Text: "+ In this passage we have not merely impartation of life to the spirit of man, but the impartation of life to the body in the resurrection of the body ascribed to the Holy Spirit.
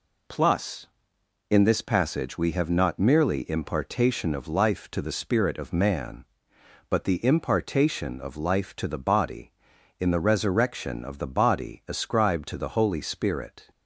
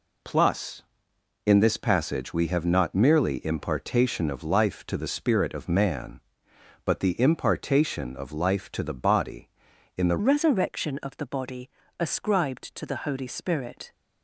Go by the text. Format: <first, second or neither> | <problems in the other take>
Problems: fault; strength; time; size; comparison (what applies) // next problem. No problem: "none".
first | changes voice at "resurrection"; from 10.1 s on; 3.8 s long // pauses between "body" and "ascribed"; slight; at 11.7 s; 0.28 s long